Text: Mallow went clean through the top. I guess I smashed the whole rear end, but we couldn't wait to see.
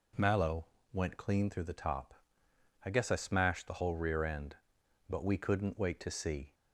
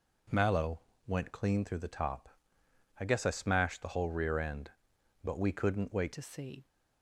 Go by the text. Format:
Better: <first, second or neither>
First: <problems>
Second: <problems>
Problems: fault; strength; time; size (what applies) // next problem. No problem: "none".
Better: first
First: pauses between "Mallow" and "went"; slight; at 0.6 s; 0.26 s long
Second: pauses between "Mallow" and "went"; slight; at 0.8 s; 0.26 s long // changes voice at "to"; from 6.1 s on; 0.5 s long